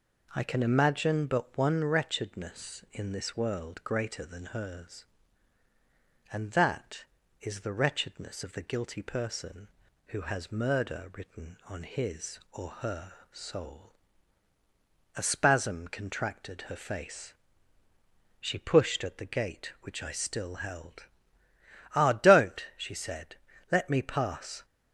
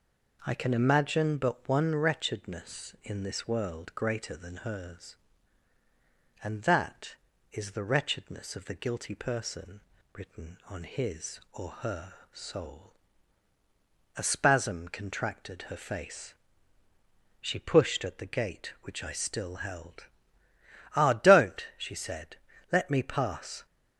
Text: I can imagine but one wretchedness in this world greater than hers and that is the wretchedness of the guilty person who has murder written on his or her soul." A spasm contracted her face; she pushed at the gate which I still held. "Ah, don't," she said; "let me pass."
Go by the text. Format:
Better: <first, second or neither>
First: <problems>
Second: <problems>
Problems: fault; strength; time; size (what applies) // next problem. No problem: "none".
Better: first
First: pauses between "her" and "soul"; slight; at 13.1 s; 0.18 s long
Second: skips "who has murder"; at 9.9 s // pauses between "her" and "soul"; slight; at 12.1 s; 0.18 s long